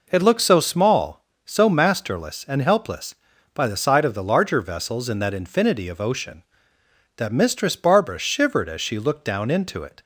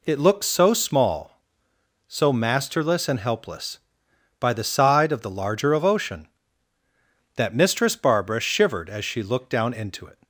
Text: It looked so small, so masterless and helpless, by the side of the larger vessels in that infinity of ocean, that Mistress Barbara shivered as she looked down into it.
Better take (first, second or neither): first